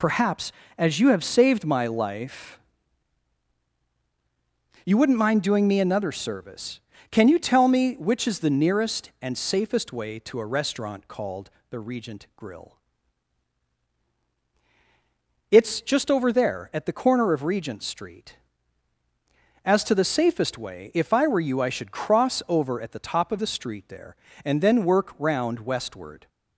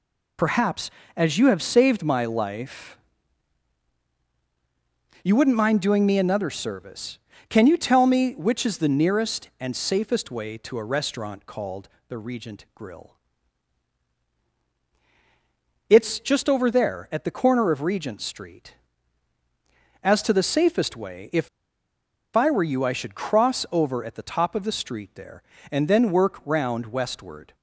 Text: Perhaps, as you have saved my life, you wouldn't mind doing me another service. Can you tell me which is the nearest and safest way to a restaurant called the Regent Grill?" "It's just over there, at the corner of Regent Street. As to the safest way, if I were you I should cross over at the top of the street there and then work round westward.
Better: first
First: pauses between "called" and "the"; slight; at 11.5 s; 0.18 s long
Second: pauses between "called" and "the"; slight; at 11.8 s; 0.18 s long // pauses between "if" and "I"; noticeable; at 21.4 s; 0.87 s long

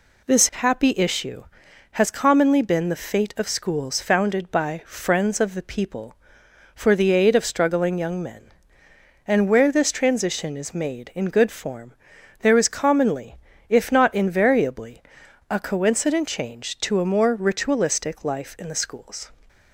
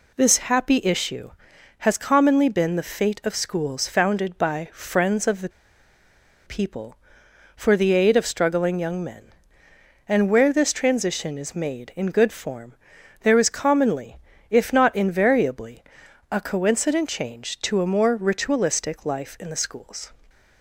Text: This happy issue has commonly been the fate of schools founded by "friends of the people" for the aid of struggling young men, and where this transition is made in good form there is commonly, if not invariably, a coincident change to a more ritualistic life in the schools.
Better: first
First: pauses between "form" and "there"; noticeable; at 11.9 s; 0.48 s long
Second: pauses between "the" and "people"; noticeable; at 5.4 s; 0.97 s long // pauses between "form" and "there"; noticeable; at 12.7 s; 0.48 s long

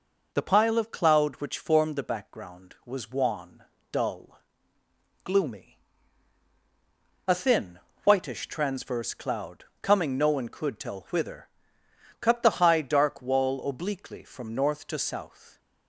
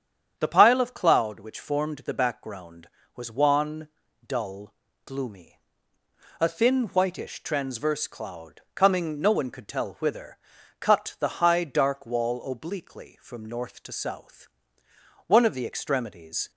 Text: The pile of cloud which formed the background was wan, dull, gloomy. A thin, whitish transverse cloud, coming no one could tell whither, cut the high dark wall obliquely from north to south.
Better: first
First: none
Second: starts louder than the rest; strong; until 1.3 s; 8.5 dB // goes on to say "One of the extremities"; noticeable; from 15.2 s on; 1.2 s long

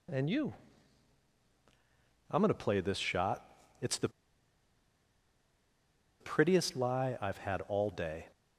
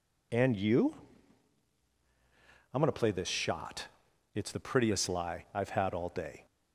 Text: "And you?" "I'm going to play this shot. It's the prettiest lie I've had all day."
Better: second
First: pauses between "the" and "prettiest"; strong; at 4.0 s; 2.1 s long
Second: none

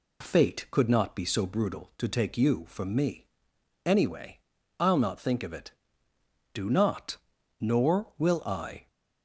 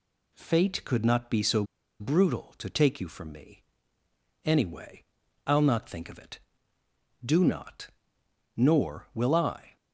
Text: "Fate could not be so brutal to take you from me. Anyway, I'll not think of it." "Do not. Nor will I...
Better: first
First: none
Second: pauses between "so" and "brutal"; at 1.6 s; 0.36 s long

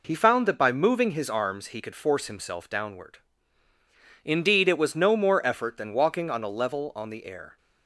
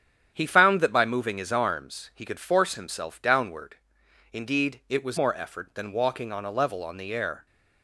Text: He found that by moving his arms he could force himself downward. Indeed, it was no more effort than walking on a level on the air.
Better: first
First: none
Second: starts louder than the rest; strong; until 1.3 s; 9 dB // skips "no"; at 5.1 s

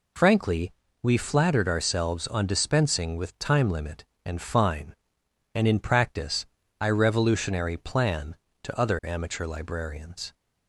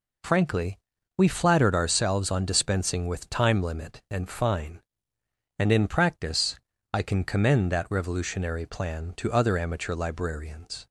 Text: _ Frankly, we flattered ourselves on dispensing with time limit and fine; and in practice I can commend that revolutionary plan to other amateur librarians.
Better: second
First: pauses between "practice" and "I"; slight; at 6.4 s; 0.36 s long // skips "can commend that"; at 6.8 s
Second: pauses between "practice" and "I"; slight; at 6.5 s; 0.36 s long

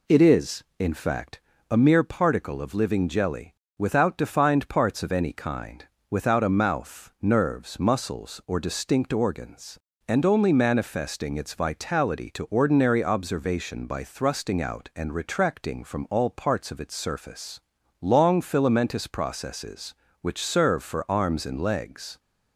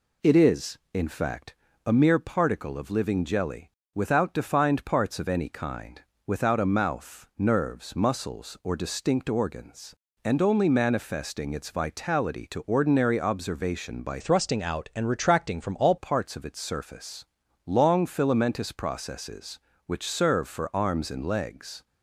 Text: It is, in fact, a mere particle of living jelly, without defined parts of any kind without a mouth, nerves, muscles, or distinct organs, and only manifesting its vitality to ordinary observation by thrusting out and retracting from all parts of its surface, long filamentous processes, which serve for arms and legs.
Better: first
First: pauses between "kind" and "without"; slight; at 5.8 s; 0.24 s long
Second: pauses between "kind" and "without"; slight; at 6.0 s; 0.24 s long // changes voice from "thrusting" to "all"; from 14.1 to 15.9 s; 1.8 s long

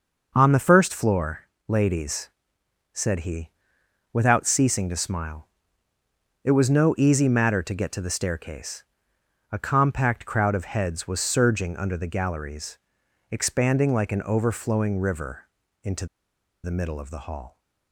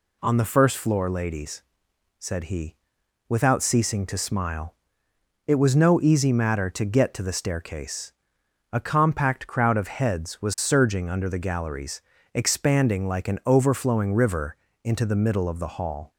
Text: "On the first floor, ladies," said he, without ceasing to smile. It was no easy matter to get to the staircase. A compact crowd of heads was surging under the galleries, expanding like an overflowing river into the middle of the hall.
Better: second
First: pauses between "river" and "into"; at 15.4 s; 0.40 s long // pauses between "into" and "the"; noticeable; at 16.0 s; 0.57 s long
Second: pauses between "river" and "into"; slight; at 14.5 s; 0.30 s long

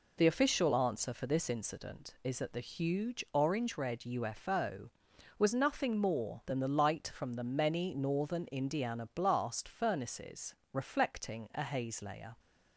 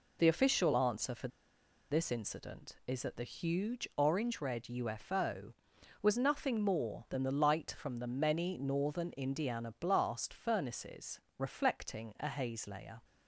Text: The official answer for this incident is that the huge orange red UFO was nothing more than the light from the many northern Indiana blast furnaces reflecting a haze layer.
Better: first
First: pauses between "furnaces" and "reflecting"; slight; at 10.5 s; 0.16 s long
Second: pauses between "for" and "this"; noticeable; at 1.2 s; 0.63 s long // pauses between "furnaces" and "reflecting"; slight; at 11.2 s; 0.16 s long

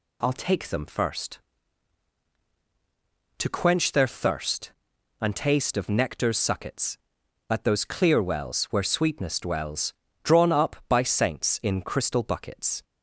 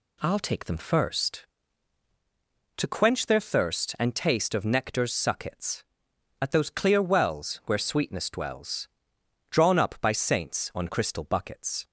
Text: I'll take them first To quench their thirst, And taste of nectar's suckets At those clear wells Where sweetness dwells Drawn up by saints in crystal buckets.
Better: first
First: pauses between "dwells" and "Drawn"; slight; at 9.9 s; 0.30 s long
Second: pauses between "dwells" and "Drawn"; noticeable; at 8.8 s; 0.62 s long // says "on" for "in"; at 10.7 s

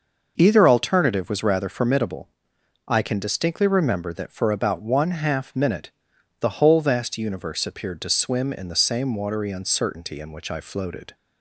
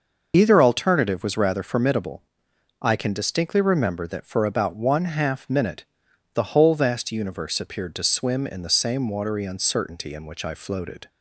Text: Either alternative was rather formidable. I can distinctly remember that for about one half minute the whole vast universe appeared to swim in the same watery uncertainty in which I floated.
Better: first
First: pauses between "minute" and "the"; noticeable; at 5.9 s; 0.50 s long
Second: loses the start of "Either"; at 0.3 s; 30 ms // pauses between "minute" and "the"; noticeable; at 5.8 s; 0.50 s long

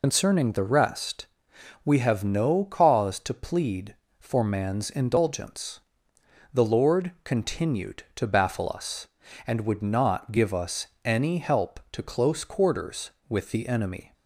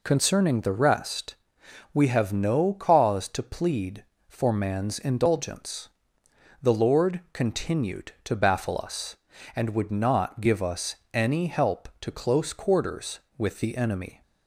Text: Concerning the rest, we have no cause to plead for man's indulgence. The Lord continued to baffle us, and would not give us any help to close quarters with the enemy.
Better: second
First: loses the start of "Concerning"; at 0.0 s; 90 ms // pauses between "us" and "any"; slight; at 10.8 s; 0.18 s long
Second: pauses between "us" and "any"; slight; at 10.9 s; 0.18 s long

